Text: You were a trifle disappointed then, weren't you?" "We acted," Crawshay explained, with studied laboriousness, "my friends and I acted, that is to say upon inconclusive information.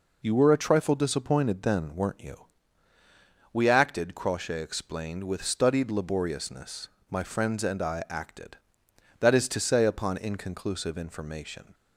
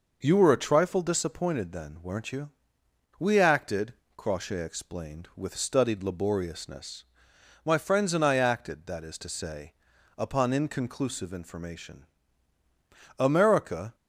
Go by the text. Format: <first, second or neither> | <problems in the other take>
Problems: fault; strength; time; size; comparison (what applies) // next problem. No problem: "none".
first | pauses between "say" and "upon"; noticeable; at 9.7 s; 0.46 s long // goes on to say "America"; noticeable; from 13.1 s on; 0.76 s long